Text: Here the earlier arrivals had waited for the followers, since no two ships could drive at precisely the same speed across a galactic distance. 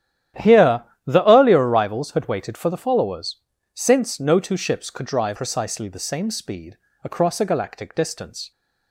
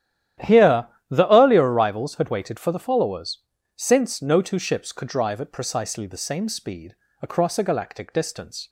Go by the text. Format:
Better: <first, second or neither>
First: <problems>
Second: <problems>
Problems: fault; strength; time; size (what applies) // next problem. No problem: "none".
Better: second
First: starts louder than the rest; strong; until 1.6 s; 11.5 dB // pauses between "Here" and "the"; slight; at 0.8 s; 0.22 s long // skips "at"; at 5.3 s // pauses between "speed" and "across"; slight; at 6.7 s; 0.28 s long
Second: starts louder than the rest; strong; until 1.6 s; 11.5 dB // pauses between "Here" and "the"; slight; at 0.8 s; 0.22 s long // pauses between "speed" and "across"; slight; at 6.9 s; 0.28 s long